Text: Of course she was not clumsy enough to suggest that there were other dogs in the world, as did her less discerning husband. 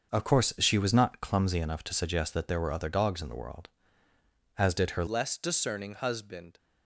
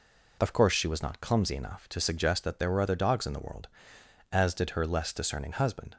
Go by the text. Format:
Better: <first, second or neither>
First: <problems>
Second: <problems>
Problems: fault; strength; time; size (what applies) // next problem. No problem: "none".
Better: second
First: starts louder than the rest; until 1.1 s; 6.5 dB // changes voice at "less"; from 5.0 s on; 1.5 s long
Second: none